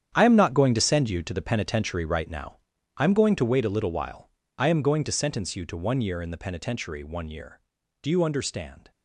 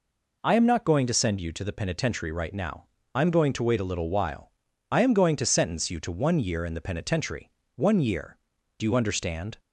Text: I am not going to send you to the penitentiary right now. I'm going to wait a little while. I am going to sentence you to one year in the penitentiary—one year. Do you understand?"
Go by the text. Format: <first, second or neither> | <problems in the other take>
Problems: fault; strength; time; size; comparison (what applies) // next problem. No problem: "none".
second | gets quieter; strong; throughout; 13 dB